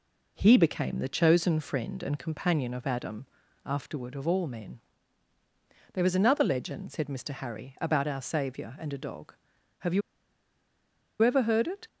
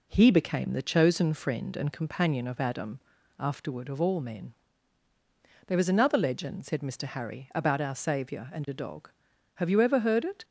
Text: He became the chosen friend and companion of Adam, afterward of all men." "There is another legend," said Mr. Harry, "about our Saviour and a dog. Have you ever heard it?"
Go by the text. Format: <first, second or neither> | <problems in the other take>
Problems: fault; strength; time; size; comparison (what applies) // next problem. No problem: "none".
second | pauses between "you" and "ever"; at 10.0 s; 1.2 s long